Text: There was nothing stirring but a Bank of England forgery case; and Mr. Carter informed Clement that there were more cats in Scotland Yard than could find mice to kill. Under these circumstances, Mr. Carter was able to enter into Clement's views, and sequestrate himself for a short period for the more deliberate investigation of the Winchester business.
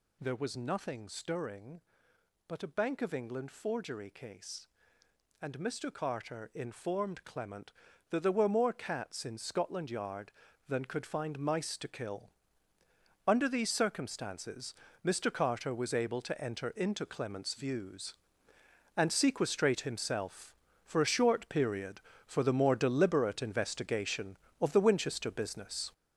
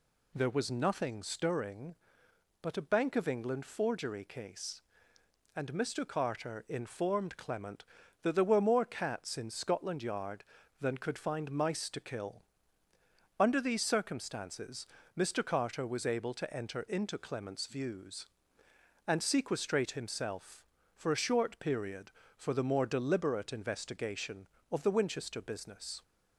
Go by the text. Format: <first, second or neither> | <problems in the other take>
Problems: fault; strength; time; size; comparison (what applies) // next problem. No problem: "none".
second | gets louder; strong; throughout; 7.5 dB